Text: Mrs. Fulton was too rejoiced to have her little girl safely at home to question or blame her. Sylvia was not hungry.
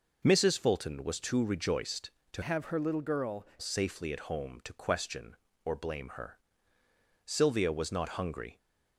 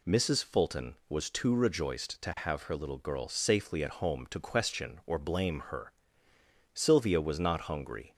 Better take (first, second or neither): second